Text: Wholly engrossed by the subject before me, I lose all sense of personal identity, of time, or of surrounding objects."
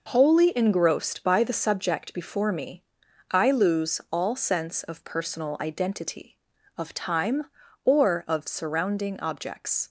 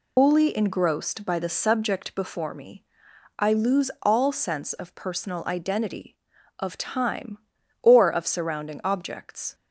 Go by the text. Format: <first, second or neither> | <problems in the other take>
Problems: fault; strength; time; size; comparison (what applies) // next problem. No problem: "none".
first | loses the start of "Wholly"; at 0.1 s; 155 ms